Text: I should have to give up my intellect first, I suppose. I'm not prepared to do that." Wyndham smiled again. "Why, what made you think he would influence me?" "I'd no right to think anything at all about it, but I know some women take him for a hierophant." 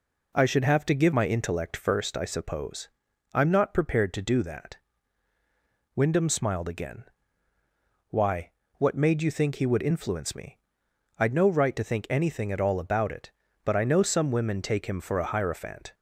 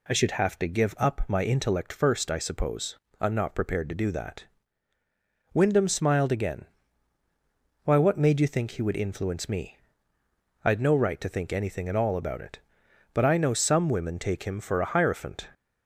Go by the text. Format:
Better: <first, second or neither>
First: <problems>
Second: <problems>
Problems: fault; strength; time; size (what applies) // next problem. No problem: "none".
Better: second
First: skips "up"; at 1.1 s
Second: none